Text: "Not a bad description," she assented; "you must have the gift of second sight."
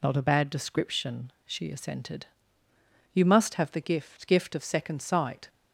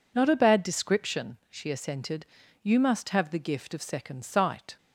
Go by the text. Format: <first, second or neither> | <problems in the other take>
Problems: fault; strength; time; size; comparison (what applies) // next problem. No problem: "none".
second | says "gift" twice; at 4.2 s